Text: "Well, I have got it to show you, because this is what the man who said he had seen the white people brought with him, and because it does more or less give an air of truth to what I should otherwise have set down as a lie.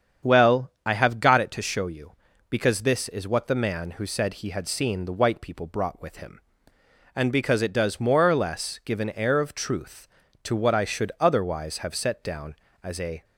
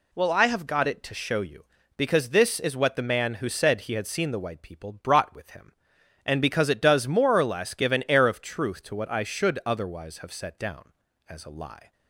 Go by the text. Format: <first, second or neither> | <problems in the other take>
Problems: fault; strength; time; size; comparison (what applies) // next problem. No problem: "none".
second | starts louder than the rest; strong; until 1.3 s; 8 dB // stops before "lie"; at 13.2 s